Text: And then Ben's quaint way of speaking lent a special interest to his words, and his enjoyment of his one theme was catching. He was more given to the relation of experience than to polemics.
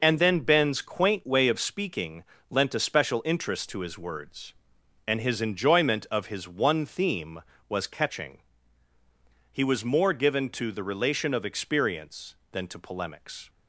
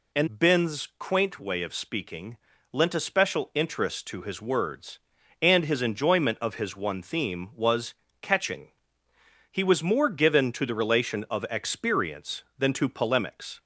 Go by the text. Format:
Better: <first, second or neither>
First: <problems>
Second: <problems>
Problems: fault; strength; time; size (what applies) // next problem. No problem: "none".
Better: first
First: pauses between "speaking" and "lent"; slight; at 2.2 s; 0.24 s long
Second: skips "then"; at 0.2 s // pauses between "speaking" and "lent"; slight; at 2.3 s; 0.36 s long // pauses between "was" and "catching"; slight; at 7.9 s; 0.28 s long